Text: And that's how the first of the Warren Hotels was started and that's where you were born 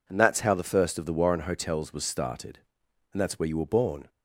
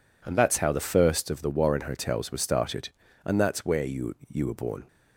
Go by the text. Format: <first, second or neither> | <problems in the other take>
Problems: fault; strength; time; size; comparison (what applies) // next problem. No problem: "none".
first | says "you" twice; at 4.2 s